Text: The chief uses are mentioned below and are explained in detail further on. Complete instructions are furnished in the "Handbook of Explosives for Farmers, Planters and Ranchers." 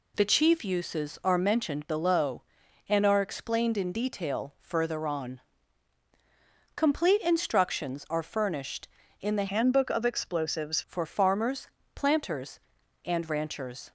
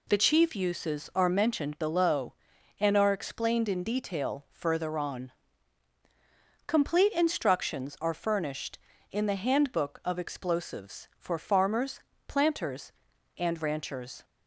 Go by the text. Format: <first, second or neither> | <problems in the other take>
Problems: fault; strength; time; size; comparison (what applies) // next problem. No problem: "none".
second | changes voice from "Handbook" to "Explosives"; from 9.4 to 10.8 s; 1.4 s long